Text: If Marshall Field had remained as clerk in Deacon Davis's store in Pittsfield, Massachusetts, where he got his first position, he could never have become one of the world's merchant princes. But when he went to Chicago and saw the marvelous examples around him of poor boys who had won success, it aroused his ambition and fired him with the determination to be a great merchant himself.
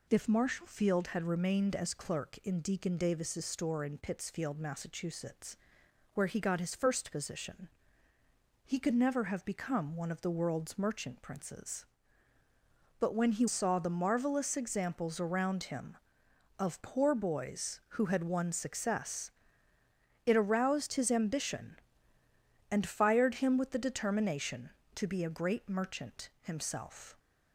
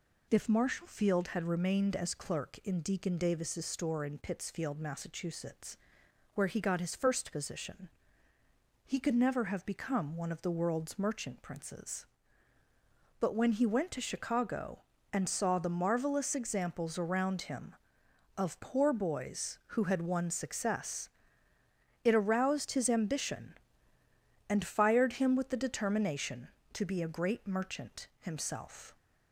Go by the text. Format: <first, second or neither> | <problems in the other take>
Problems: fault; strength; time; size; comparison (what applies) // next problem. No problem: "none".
second | skips "went to Chicago and"; at 13.4 s